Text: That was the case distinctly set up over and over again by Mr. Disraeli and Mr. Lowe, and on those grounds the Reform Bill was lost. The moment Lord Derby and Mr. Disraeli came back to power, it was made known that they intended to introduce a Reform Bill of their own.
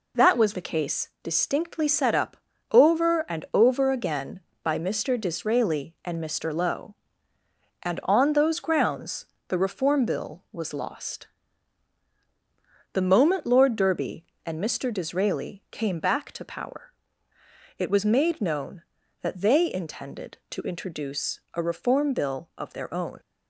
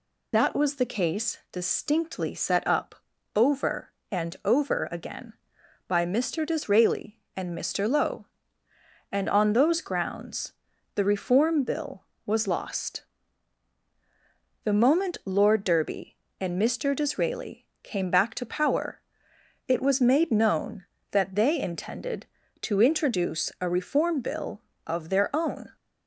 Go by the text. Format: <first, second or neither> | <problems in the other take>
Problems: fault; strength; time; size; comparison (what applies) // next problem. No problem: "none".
first | loses the start of "That"; at 0.3 s; 40 ms // pauses between "up" and "over"; at 2.9 s; 0.40 s long; slight in the first // pauses between "grounds" and "the"; at 10.5 s; 0.42 s long; slight in the first // pauses between "Disraeli" and "came"; slight; at 17.6 s; 0.16 s long